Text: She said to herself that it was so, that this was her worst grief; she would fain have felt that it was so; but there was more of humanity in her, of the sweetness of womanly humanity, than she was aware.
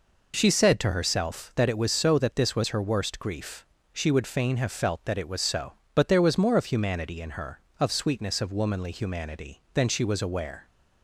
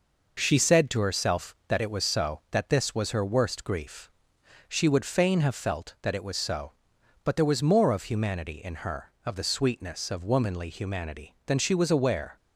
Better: second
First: skips "the"; at 7.9 s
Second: none

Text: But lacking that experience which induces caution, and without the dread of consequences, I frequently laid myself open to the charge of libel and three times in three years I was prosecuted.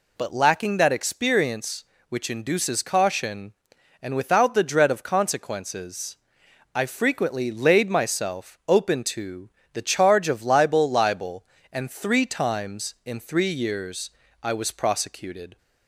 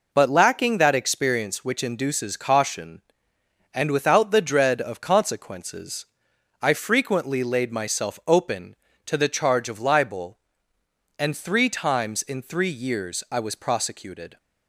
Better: second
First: pauses between "to" and "the"; slight; at 9.4 s; 0.24 s long // says "libel" twice; at 10.8 s // pauses between "years" and "I"; slight; at 14.0 s; 0.32 s long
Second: none

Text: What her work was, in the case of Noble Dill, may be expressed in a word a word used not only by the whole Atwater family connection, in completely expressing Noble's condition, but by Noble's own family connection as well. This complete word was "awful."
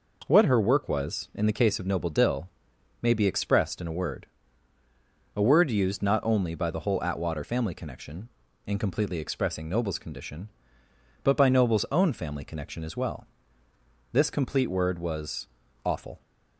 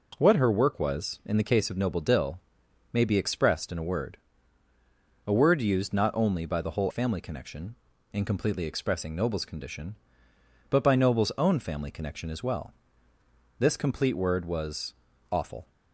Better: first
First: pauses between "word" and "a"; at 4.2 s; 1.0 s long // pauses between "was" and "awful"; at 15.4 s; 0.38 s long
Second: pauses between "word" and "a"; at 4.1 s; 1.0 s long // skips "Atwater"; at 6.9 s // pauses between "was" and "awful"; at 14.9 s; 0.38 s long

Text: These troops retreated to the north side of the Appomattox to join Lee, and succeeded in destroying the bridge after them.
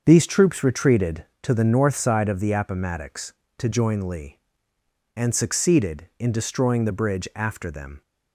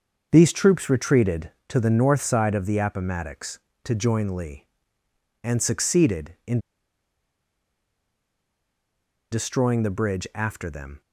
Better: first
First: starts louder than the rest; until 1.0 s; 6.5 dB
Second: starts louder than the rest; until 1.3 s; 6.5 dB // pauses between "in" and "destroying"; strong; at 6.6 s; 2.7 s long

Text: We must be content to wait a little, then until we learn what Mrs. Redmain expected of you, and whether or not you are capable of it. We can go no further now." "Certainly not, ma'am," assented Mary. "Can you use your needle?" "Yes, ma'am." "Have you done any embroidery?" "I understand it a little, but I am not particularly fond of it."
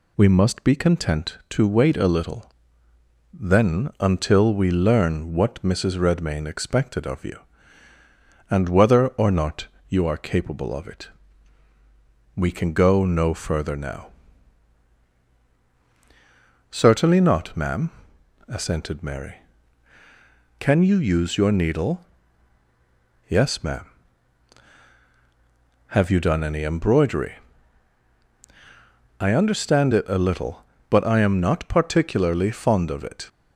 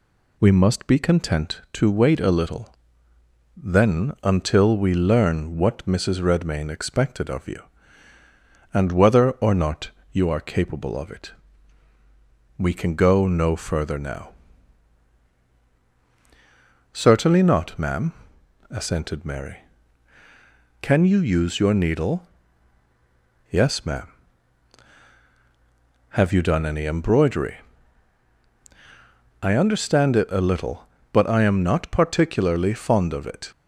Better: neither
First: pauses between "not" and "you"; slight; at 9.6 s; 0.22 s long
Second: pauses between "not" and "you"; slight; at 9.8 s; 0.22 s long

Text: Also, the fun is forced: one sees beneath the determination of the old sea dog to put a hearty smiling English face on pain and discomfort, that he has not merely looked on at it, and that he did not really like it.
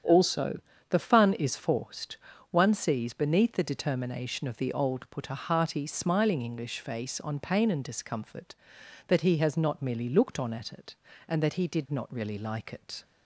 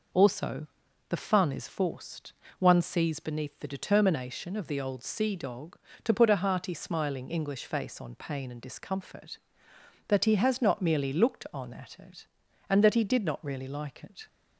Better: second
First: starts louder than the rest; strong; until 1.3 s; 8.5 dB // skips "sea dog to"; at 5.0 s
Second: none

